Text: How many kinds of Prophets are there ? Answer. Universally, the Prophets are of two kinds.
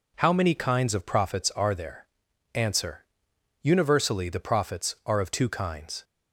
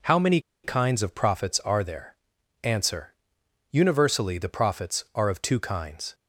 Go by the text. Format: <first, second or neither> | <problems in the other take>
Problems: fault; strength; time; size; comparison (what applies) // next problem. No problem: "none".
first | pauses between "many" and "kinds"; slight; at 0.4 s; 0.23 s long